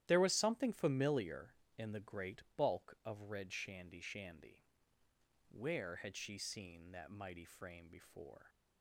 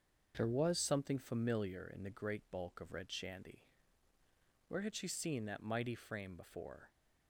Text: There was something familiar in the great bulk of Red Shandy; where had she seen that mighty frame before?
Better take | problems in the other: second | starts louder than the rest; strong; until 1.0 s; 12.5 dB; also in the second // pauses between "great" and "bulk"; slight; at 2.4 s; 0.16 s long // says "Shandy" twice; at 4.0 s

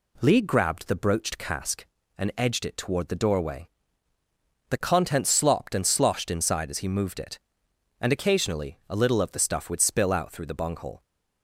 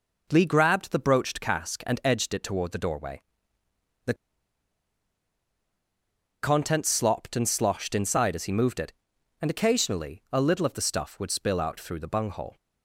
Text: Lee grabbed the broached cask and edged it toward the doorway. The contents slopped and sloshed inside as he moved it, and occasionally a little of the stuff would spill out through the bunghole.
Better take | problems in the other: first | pauses between "The" and "contents"; strong; at 4.1 s; 2.2 s long

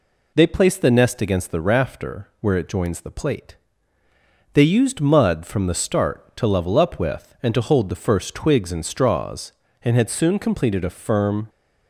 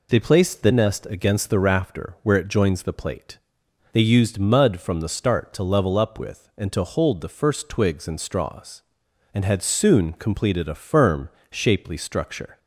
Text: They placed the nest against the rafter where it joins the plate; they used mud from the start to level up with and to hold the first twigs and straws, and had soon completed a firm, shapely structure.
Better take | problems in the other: second | stops before "shapely structure"; at 11.4 s

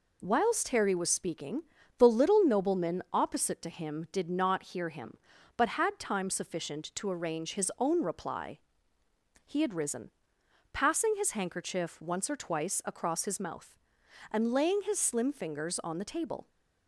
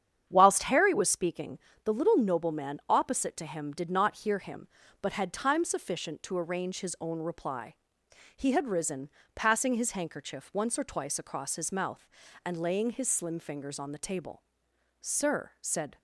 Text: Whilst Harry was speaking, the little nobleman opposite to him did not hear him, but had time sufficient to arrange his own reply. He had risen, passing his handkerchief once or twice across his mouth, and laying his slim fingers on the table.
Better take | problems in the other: first | starts louder than the rest; strong; until 1.3 s; 9 dB // goes on to say "Sir said"; noticeable; from 15.0 s on; 0.96 s long

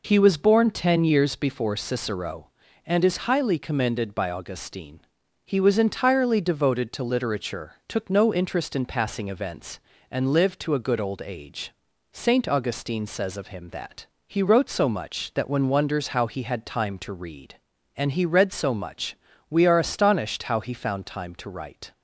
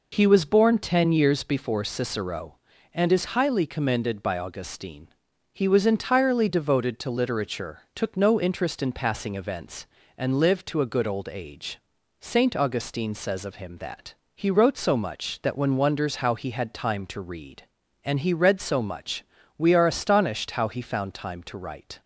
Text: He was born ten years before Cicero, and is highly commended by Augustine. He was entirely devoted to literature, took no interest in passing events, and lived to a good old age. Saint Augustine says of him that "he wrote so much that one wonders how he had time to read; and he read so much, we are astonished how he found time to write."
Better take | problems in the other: neither | pauses between "that" and "he"; slight; the same in both

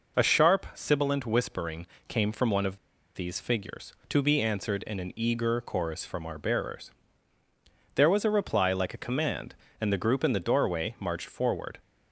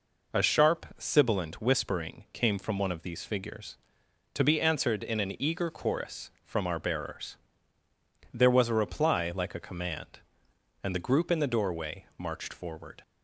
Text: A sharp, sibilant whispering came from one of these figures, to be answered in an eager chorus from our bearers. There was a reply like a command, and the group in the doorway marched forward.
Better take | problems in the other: second | pauses between "whispering" and "came"; slight; at 1.8 s; 0.20 s long // pauses between "of" and "these"; at 2.7 s; 0.38 s long

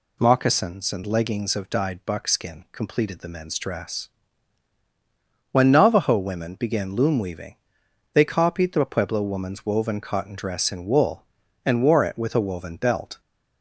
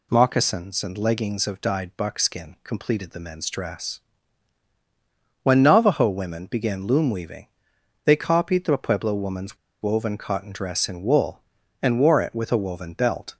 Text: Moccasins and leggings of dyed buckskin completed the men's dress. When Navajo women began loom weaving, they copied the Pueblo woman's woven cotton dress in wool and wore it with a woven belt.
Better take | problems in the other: first | pauses between "woman's" and "woven"; slight; at 9.5 s; 0.25 s long

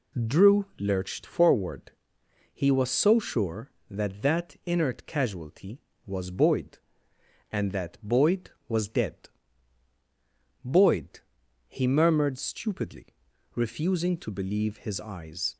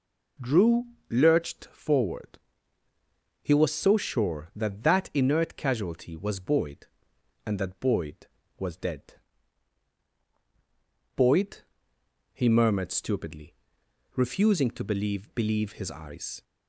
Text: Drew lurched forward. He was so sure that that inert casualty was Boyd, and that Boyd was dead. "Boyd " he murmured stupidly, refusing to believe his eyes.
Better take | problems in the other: first | pauses between "Drew" and "lurched"; slight; at 0.8 s; 0.24 s long // says "believe" twice; at 15.3 s

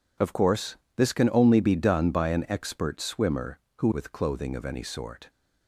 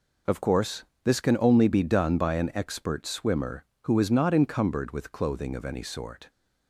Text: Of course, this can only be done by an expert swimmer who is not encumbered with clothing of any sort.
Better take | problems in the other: second | skips "is not encumbered"; at 3.9 s

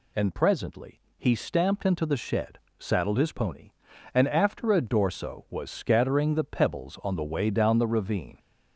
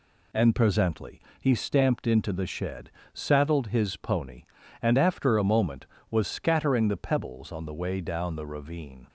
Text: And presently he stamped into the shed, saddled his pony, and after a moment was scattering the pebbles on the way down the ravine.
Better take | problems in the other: second | pauses between "presently" and "he"; slight; at 0.9 s; 0.18 s long; slight in the second // says "dorso" for "moment"; at 4.7 s

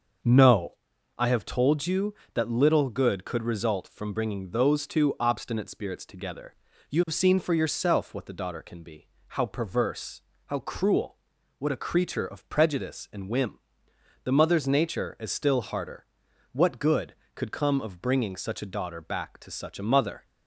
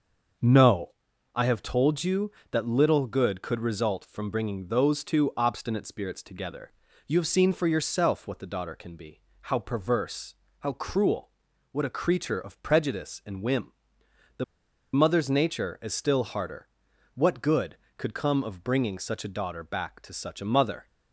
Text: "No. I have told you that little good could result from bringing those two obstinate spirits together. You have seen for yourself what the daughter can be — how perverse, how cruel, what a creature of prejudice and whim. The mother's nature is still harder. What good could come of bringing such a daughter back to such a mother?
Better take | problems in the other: first | starts louder than the rest; until 1.8 s; 6 dB; also in the first // pauses between "The" and "mother's"; noticeable; at 14.4 s; 0.50 s long

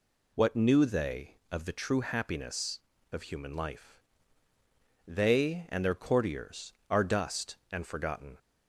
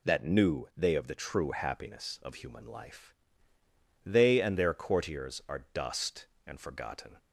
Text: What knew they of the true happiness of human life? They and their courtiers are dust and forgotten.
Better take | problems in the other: first | says "That" for "What"; at 0.0 s

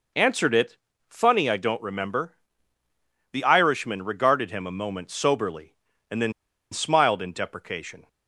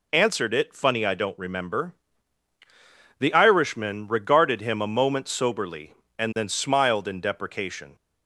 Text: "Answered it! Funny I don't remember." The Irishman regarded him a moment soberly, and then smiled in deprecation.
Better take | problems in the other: second | pauses between "then" and "smiled"; at 6.3 s; 0.41 s long

